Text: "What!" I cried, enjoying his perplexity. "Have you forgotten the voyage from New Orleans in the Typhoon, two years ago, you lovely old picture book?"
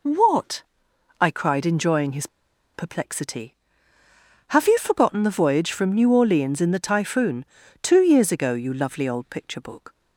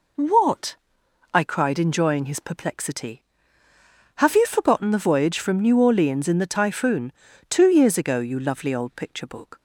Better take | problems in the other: second | pauses between "his" and "perplexity"; noticeable; at 2.2 s; 0.48 s long

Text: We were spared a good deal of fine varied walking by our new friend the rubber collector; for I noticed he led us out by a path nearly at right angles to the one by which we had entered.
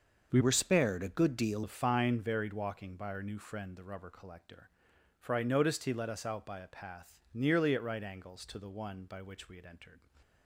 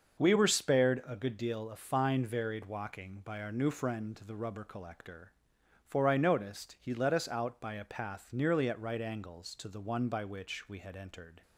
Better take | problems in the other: second | starts louder than the rest; until 1.3 s; 6.5 dB; also in the second // changes voice from "were" to "deal"; from 0.3 to 1.6 s; 1.3 s long

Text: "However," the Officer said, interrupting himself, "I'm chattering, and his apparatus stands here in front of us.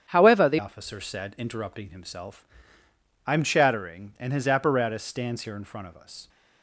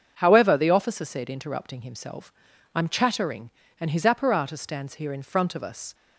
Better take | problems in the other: second | starts louder than the rest; strong; until 1.0 s; 8.5 dB; also in the second // changes voice at "Officer"; from 0.5 s on; 5.7 s long

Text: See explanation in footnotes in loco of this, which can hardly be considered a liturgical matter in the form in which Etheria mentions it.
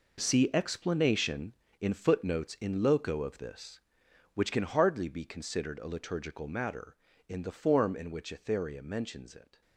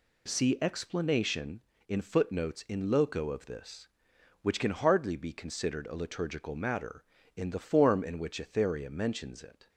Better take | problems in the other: second | gets quieter; strong; throughout; 11.5 dB

